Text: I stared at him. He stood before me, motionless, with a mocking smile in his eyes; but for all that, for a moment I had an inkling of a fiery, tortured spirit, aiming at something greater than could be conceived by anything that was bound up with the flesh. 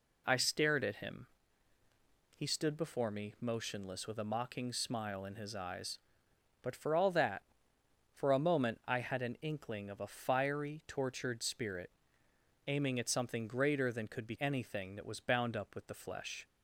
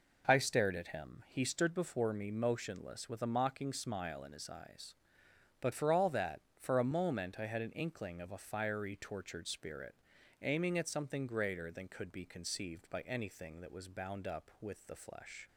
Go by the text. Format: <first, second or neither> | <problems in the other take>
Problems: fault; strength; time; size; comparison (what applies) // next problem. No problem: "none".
second | skips "conceived by"; at 14.3 s